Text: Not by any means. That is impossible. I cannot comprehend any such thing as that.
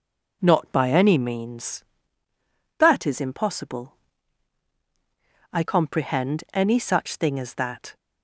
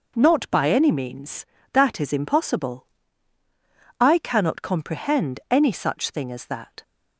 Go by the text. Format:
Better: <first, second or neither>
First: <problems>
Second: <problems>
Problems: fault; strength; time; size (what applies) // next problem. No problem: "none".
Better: second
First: skips "cannot"; at 5.6 s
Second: none